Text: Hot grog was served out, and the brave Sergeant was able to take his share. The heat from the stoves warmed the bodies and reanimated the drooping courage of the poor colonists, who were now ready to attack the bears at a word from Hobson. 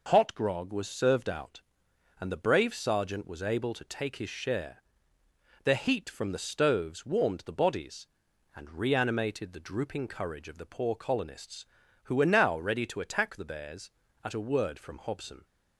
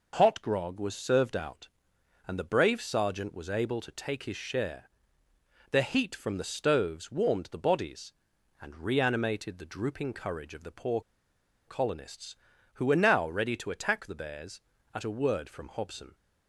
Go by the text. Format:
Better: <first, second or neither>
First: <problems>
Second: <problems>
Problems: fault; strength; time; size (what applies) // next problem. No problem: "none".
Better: first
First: none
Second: pauses between "poor" and "colonists"; noticeable; at 11.0 s; 0.67 s long